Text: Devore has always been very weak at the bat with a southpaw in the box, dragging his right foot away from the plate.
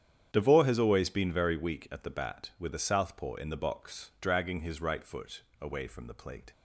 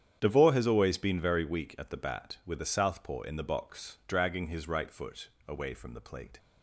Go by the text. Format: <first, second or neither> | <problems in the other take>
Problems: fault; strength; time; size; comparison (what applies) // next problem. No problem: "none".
neither | starts louder than the rest; strong; the same in both // pauses between "foot" and "away"; slight; the same in both